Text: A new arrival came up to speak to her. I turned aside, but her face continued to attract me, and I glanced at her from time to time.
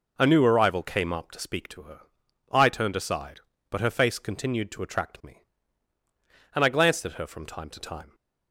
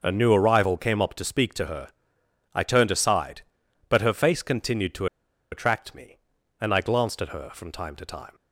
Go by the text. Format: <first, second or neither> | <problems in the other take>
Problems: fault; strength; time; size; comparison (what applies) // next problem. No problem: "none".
first | pauses between "to" and "attract"; noticeable; at 5.0 s; 0.46 s long